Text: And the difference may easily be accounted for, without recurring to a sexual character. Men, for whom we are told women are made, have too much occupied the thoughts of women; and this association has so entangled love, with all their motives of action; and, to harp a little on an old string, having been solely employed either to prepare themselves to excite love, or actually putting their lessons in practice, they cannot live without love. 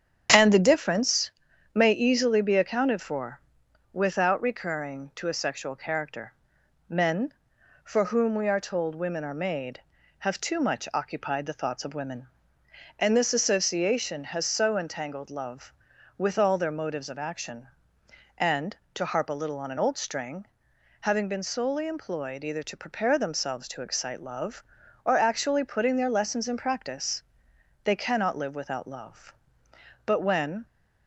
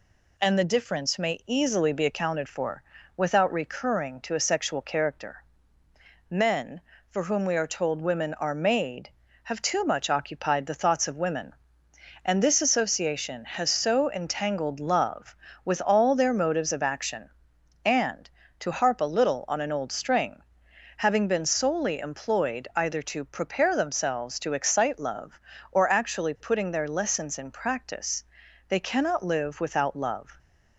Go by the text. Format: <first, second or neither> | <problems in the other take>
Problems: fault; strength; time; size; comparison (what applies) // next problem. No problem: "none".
second | starts louder than the rest; strong; until 1.7 s; 8.5 dB // pauses between "difference" and "may"; at 1.3 s; 0.44 s long // goes on to say "But when"; from 30.0 s on; 0.60 s long